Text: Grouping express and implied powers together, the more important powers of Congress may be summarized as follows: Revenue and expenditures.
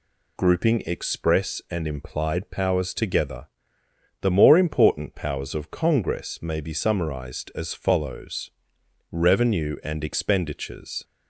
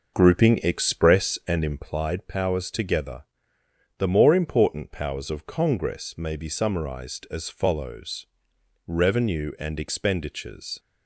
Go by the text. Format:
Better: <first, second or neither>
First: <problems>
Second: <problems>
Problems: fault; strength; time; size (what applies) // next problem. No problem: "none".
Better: first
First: none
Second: starts louder than the rest; noticeable; until 1.8 s; 6 dB